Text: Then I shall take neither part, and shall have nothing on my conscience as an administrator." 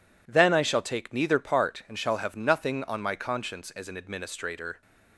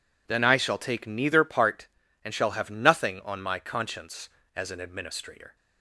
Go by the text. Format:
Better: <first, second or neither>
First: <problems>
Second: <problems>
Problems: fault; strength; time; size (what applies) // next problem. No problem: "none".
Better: neither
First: none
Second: none